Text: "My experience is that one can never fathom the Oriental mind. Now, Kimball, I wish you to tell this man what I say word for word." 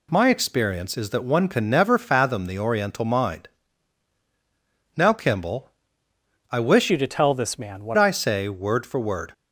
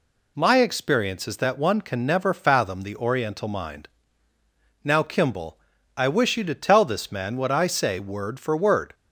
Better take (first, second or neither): second